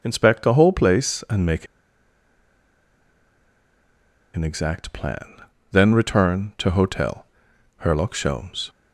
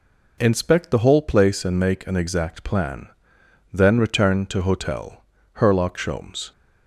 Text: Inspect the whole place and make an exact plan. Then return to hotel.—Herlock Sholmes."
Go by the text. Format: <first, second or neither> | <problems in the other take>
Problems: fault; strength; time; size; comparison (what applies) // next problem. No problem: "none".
second | pauses between "make" and "an"; strong; at 1.6 s; 2.6 s long